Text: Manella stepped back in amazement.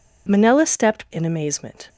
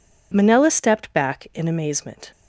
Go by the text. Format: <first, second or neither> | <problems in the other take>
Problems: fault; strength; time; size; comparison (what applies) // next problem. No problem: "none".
second | skips "back"; at 1.0 s